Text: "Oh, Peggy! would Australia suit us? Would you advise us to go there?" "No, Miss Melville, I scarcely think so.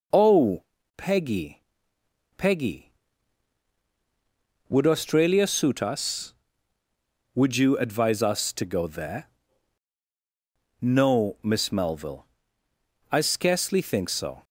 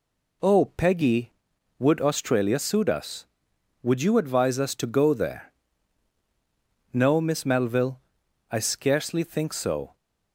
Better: second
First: says "Peggy" twice; at 2.3 s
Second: none

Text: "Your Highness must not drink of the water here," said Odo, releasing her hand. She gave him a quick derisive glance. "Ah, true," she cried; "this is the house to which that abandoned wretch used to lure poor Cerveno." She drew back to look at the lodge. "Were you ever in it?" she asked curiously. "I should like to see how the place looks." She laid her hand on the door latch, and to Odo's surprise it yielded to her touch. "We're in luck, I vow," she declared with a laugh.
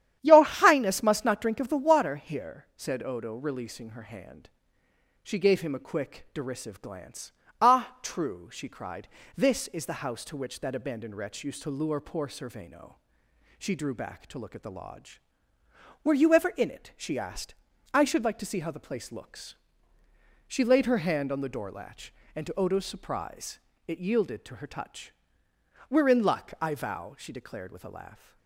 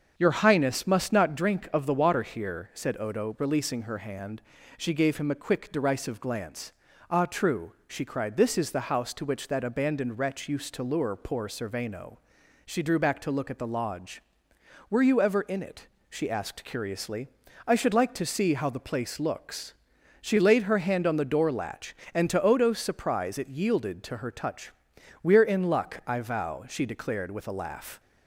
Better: second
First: starts louder than the rest; strong; until 1.2 s; 10.5 dB // skips "curiously"; at 17.7 s // pauses between "surprise" and "it"; slight; at 23.5 s; 0.28 s long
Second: starts louder than the rest; until 1.1 s; 7 dB

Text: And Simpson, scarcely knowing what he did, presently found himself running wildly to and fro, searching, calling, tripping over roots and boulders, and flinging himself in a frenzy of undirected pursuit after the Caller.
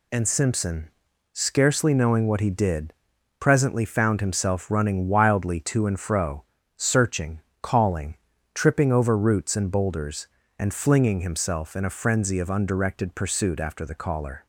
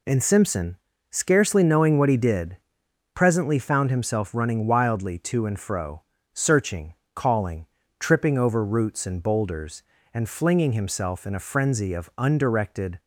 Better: first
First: none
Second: stops before "pursuit after the Caller"; at 12.9 s

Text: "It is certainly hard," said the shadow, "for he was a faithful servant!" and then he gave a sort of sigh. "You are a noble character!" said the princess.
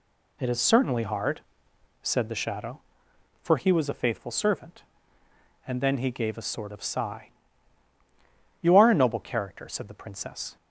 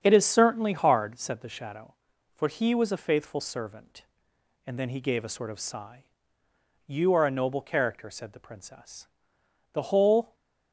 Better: first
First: none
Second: starts louder than the rest; strong; until 1.0 s; 7.5 dB // goes on to say "The whole"; from 9.7 s on; 0.60 s long

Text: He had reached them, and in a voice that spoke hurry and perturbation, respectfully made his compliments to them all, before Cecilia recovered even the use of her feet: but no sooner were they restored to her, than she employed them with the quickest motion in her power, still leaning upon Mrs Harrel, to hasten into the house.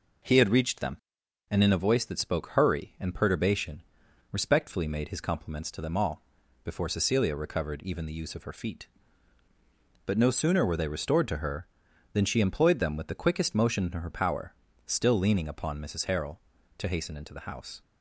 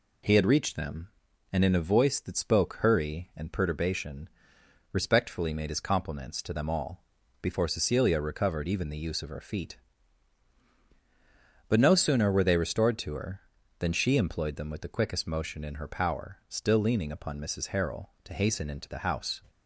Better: neither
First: none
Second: none

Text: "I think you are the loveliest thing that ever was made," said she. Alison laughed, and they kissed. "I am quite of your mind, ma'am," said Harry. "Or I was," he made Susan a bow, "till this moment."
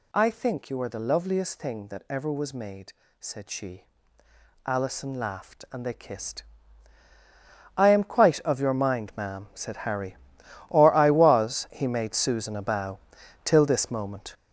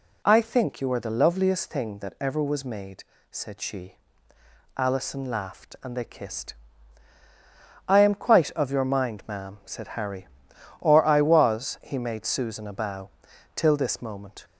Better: second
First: gets louder; strong; throughout; 7.5 dB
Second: none

